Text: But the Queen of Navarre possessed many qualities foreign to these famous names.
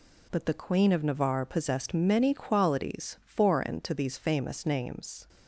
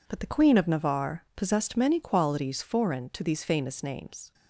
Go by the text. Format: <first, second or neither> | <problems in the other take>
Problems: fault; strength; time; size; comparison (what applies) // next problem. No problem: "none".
neither | none